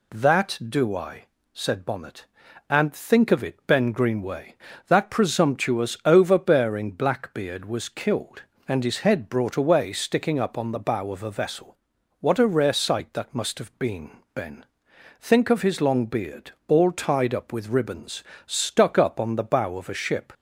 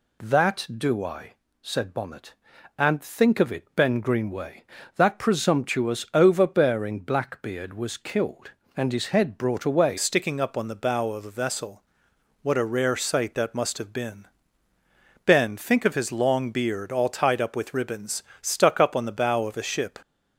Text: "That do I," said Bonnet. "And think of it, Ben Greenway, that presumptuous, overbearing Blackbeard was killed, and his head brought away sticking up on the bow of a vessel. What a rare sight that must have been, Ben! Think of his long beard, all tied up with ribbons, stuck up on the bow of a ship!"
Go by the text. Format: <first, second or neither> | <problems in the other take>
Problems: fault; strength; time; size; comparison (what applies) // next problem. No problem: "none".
first | changes voice at "sticking"; from 9.9 s on; 10.0 s long